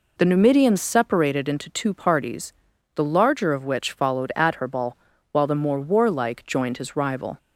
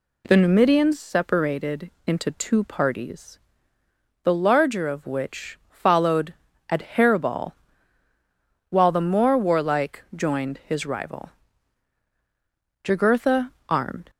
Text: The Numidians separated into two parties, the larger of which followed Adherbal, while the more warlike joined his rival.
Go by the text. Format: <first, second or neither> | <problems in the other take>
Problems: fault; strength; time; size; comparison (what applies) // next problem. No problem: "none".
first | pauses between "separated" and "into"; slight; at 1.9 s; 0.16 s long // pauses between "followed" and "Adherbal"; slight; at 6.3 s; 0.34 s long // goes on to say "Jugurtha armed"; noticeable; from 12.8 s on; 1.2 s long